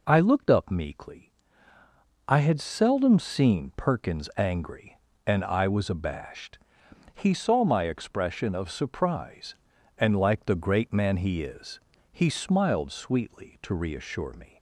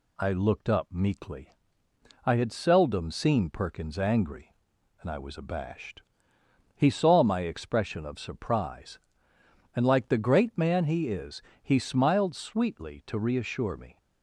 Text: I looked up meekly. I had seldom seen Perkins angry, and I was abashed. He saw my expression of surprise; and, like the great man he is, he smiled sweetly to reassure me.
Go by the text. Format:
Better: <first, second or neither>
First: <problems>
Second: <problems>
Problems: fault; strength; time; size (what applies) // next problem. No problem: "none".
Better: neither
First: none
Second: none